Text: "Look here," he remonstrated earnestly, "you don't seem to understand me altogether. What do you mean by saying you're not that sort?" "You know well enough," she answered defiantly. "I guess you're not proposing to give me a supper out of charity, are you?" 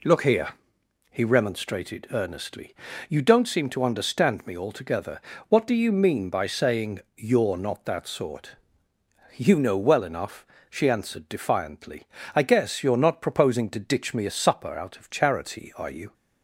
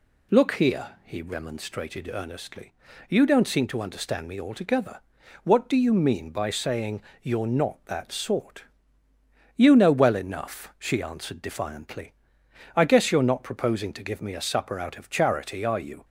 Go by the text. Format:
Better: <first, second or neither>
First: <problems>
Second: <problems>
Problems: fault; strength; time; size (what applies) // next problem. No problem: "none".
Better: second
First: pauses between "saying" and "you're"; slight; at 7.0 s; 0.16 s long // says "ditch" for "give"; at 13.7 s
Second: pauses between "saying" and "you're"; slight; at 7.0 s; 0.22 s long